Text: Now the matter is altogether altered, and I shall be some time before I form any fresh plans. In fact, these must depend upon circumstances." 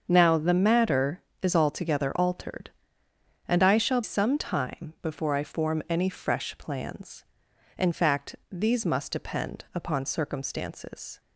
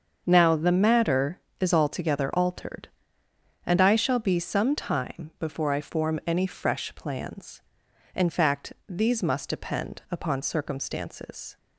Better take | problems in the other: second | starts louder than the rest; until 1.0 s; 6.5 dB; also in the second // skips "be"; at 4.0 s

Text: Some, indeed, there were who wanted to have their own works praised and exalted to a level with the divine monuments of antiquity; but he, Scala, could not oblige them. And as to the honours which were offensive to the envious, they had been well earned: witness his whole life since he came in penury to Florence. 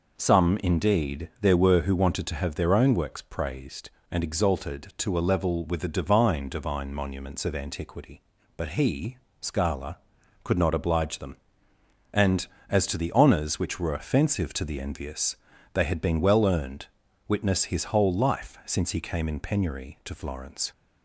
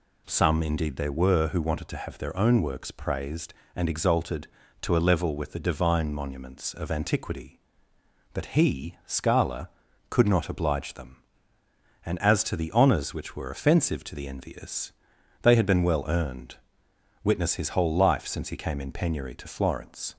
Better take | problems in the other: second | says "divine" twice; at 6.4 s

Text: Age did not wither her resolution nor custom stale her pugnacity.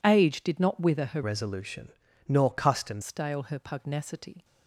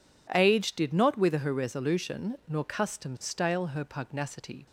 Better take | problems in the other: second | changes voice from "resolution" to "custom"; from 1.2 to 3.0 s; 1.8 s long // pauses between "resolution" and "nor"; slight; at 1.9 s; 0.36 s long

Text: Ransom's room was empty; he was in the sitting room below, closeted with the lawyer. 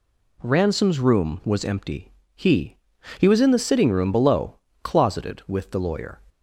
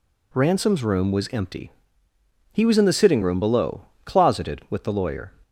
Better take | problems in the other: second | says "he" twice; at 3.1 s

